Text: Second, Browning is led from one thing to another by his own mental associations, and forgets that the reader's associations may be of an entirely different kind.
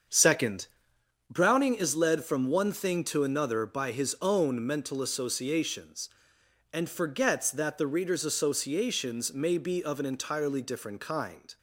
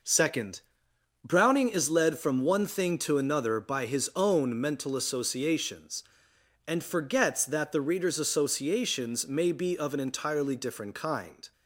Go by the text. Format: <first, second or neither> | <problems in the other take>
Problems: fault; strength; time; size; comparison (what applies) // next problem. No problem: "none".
second | starts louder than the rest; until 1.0 s; 7 dB